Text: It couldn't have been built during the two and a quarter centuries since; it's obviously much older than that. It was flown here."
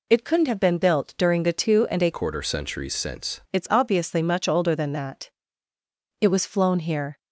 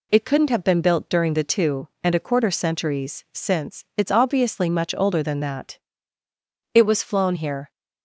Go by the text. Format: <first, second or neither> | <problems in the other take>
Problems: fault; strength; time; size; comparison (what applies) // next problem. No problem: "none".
second | changes voice from "quarter" to "since"; from 2.1 to 3.3 s; 1.2 s long